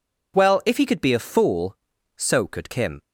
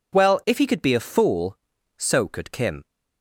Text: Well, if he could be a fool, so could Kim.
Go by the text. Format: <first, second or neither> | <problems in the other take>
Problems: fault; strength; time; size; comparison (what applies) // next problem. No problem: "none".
neither | none